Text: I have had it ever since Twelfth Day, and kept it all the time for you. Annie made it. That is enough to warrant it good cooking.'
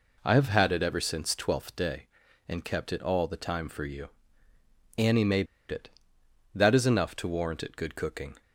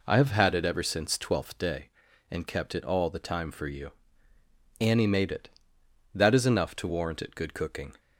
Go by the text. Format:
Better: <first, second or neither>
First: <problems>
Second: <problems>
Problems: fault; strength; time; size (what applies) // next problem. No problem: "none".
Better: second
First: pauses between "made" and "it"; slight; at 5.4 s; 0.25 s long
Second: none